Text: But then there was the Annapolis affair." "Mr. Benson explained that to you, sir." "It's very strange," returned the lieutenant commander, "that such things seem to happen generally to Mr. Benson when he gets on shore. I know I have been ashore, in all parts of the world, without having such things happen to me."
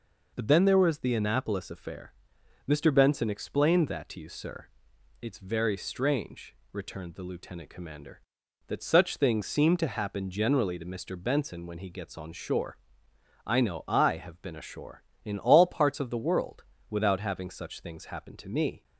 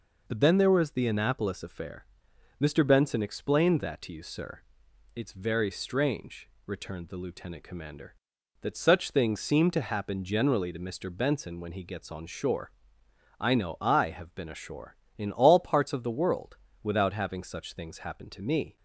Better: neither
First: none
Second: none

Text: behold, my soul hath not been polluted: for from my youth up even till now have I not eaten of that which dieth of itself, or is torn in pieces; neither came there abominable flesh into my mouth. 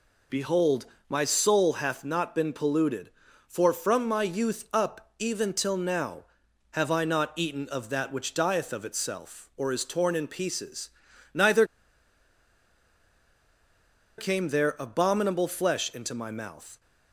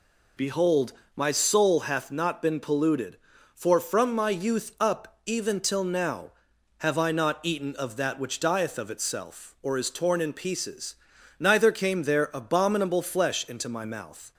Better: second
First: pauses between "neither" and "came"; strong; at 11.6 s; 2.5 s long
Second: none

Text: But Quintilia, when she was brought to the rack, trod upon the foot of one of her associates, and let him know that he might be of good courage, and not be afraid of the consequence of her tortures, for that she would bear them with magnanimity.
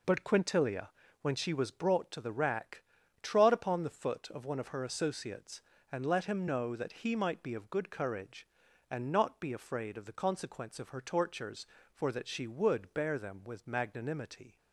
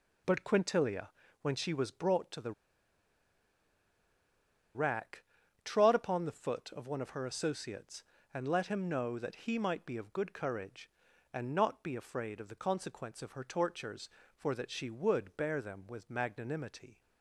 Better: first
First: none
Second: pauses between "the" and "rack"; strong; at 2.5 s; 2.2 s long

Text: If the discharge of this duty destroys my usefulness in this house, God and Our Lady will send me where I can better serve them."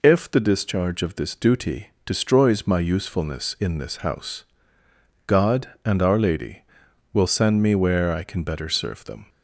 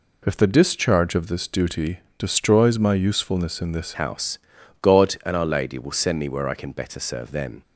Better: first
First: pauses between "duty" and "destroys"; slight; at 1.9 s; 0.16 s long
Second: pauses between "duty" and "destroys"; slight; at 1.9 s; 0.18 s long // changes voice at "house"; from 3.9 s on; 3.7 s long

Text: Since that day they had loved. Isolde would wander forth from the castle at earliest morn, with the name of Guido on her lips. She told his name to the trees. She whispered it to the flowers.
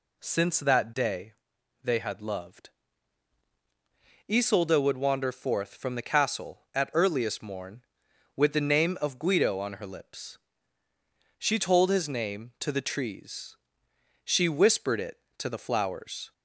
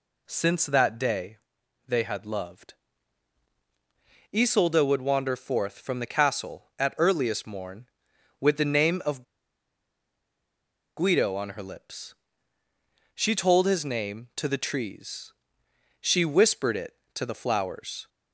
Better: first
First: pauses between "day" and "they"; noticeable; at 1.3 s; 0.50 s long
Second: pauses between "day" and "they"; noticeable; at 1.3 s; 0.50 s long // pauses between "of" and "Guido"; strong; at 9.2 s; 1.7 s long

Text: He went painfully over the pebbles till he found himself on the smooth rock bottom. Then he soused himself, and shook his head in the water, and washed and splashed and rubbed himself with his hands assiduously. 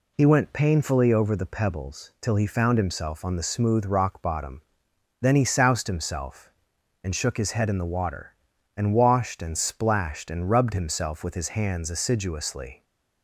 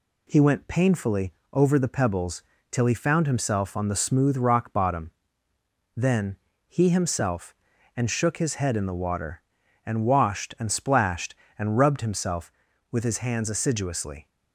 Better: first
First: none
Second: pauses between "painfully" and "over"; slight; at 1.3 s; 0.22 s long // pauses between "pebbles" and "till"; slight; at 2.4 s; 0.28 s long // pauses between "Then" and "he"; slight; at 6.3 s; 0.32 s long // skips "soused"; at 6.8 s

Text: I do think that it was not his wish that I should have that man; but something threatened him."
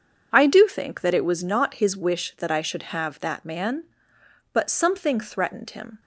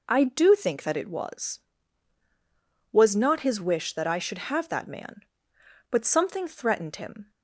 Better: first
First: none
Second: says "was" twice; at 2.9 s

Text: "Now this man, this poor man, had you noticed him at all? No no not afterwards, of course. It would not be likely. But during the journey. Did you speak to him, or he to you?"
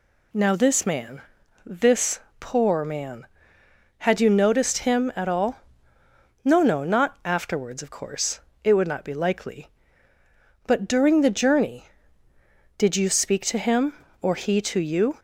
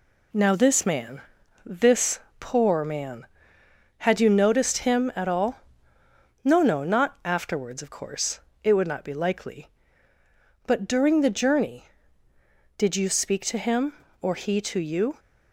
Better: first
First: pauses between "this" and "poor"; slight; at 2.1 s; 0.20 s long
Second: gets quieter; noticeable; throughout; 4 dB // pauses between "this" and "poor"; slight; at 2.1 s; 0.20 s long

